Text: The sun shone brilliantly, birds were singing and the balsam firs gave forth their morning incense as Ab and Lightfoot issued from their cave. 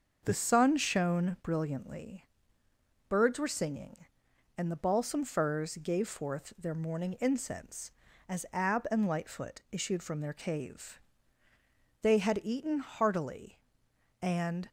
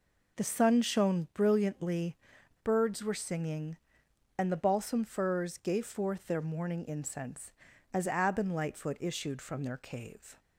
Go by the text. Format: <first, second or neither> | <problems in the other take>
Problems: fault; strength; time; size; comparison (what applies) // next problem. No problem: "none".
second | starts louder than the rest; until 1.2 s; 6.5 dB // goes on to say "They had eaten heartily and"; strong; from 12.0 s on; 2.6 s long